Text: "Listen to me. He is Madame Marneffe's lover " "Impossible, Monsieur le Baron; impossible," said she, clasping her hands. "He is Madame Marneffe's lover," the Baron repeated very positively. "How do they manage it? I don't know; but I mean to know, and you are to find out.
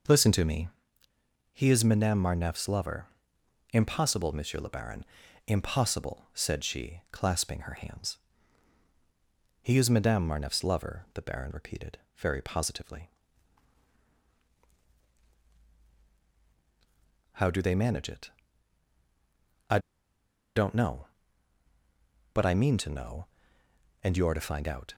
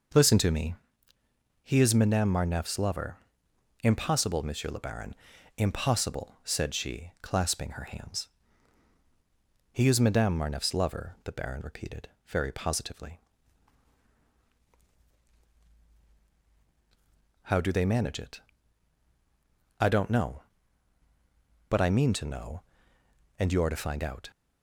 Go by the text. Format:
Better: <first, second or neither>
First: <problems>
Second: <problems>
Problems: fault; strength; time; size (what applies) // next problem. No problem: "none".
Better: second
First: pauses between "repeated" and "very"; slight; at 11.9 s; 0.20 s long // pauses between "I" and "don't"; noticeable; at 19.8 s; 0.75 s long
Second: pauses between "repeated" and "very"; slight; at 12.0 s; 0.20 s long